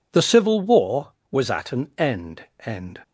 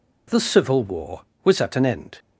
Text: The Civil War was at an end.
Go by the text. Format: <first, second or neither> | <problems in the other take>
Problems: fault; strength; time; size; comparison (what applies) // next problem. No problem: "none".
second | says "end" twice; at 2.6 s